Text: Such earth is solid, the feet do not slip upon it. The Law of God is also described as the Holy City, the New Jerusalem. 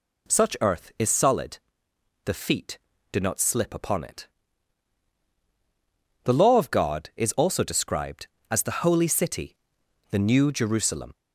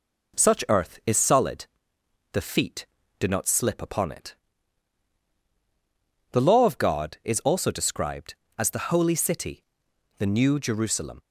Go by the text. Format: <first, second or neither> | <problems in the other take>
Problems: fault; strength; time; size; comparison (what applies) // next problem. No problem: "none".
first | gets quieter; slight; throughout; 2 dB